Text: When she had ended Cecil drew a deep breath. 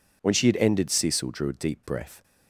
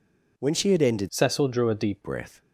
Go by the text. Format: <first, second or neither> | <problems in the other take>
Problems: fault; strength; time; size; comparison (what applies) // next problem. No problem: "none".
first | changes voice from "Cecil" to "deep"; from 1.0 to 2.0 s; 1.0 s long